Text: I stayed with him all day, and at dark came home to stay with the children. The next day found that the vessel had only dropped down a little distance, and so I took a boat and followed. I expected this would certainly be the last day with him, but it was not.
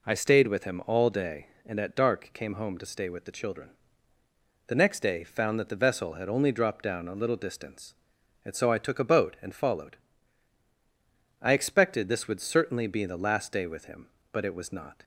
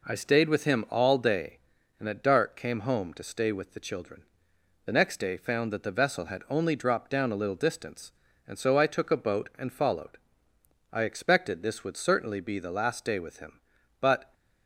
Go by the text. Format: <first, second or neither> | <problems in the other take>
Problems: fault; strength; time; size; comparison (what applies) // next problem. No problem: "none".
first | stops before "it was not"; at 14.3 s